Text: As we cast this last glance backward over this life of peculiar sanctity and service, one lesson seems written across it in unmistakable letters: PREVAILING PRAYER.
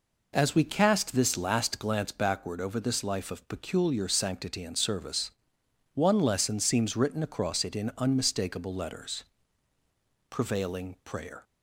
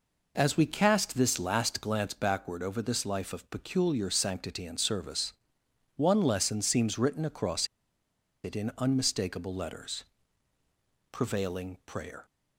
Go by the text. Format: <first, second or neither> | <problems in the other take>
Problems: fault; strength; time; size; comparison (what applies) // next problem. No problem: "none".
first | pauses between "across" and "it"; noticeable; at 7.6 s; 0.77 s long